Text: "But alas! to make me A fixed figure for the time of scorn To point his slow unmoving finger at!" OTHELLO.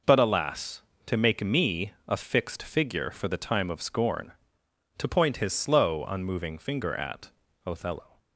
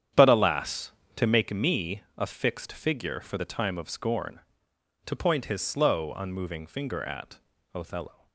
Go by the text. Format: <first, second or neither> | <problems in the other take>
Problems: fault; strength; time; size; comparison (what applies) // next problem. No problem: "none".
first | starts louder than the rest; strong; until 1.5 s; 9 dB // pauses between "me" and "A"; slight; at 2.0 s; 0.16 s long; slight in the first